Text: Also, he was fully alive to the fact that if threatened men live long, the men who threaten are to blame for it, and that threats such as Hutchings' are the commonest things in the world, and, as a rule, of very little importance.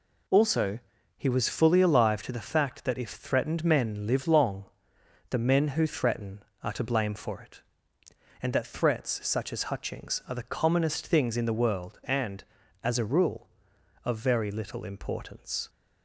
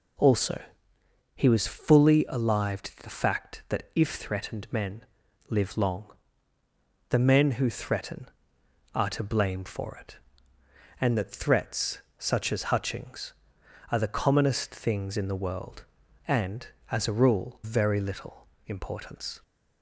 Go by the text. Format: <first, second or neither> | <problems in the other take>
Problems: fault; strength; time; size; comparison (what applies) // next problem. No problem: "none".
first | pauses between "men" and "live"; noticeable; at 5.0 s; 0.48 s long // pauses between "threats" and "such"; slight; at 11.9 s; 0.18 s long // skips "of"; at 17.6 s // pauses between "little" and "importance"; slight; at 18.4 s; 0.20 s long